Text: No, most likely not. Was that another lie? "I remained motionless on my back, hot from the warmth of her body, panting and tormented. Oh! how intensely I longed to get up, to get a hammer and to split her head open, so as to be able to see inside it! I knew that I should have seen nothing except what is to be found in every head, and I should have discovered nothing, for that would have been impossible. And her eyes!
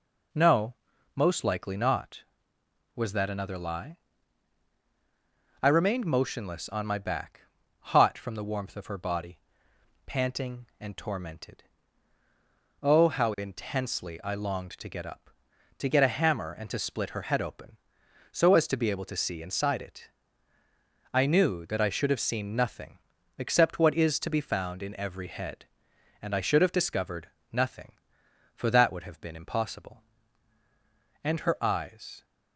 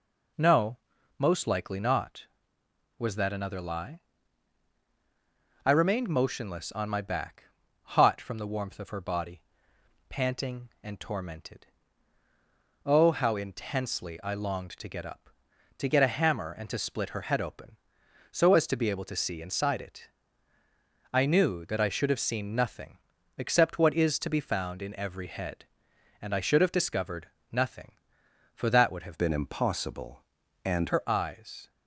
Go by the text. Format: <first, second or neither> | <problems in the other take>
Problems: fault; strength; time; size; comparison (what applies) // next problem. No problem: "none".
first | pauses between "nothing" and "except"; at 22.9 s; 0.40 s long; also in the first // pauses between "discovered" and "nothing"; slight; at 27.2 s; 0.24 s long; slight in the first // changes voice from "been" to "And"; from 29.1 to 30.9 s; 1.8 s long